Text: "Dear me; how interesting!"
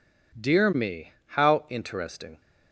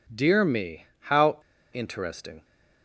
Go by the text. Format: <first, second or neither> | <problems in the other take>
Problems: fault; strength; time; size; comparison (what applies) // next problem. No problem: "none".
first | pauses between "how" and "interesting"; slight; at 1.3 s; 0.35 s long